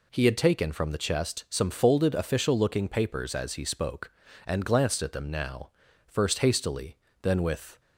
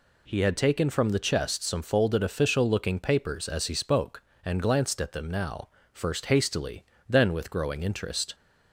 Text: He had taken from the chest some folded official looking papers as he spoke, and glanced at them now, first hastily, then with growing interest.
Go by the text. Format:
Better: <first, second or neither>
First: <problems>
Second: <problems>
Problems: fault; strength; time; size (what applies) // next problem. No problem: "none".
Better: second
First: stops before "growing interest"; at 7.7 s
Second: none